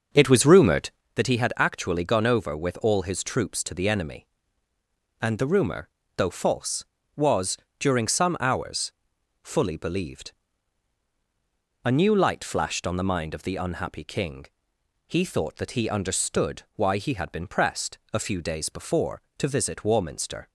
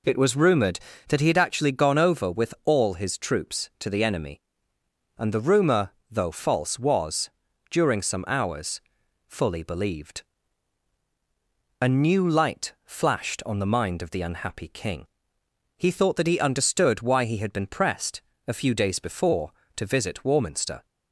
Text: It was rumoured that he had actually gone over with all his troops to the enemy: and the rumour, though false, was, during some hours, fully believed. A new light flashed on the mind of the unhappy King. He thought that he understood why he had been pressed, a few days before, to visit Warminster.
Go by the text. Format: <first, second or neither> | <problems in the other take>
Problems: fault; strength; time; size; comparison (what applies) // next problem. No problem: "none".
second | starts louder than the rest; noticeable; until 1.1 s; 6 dB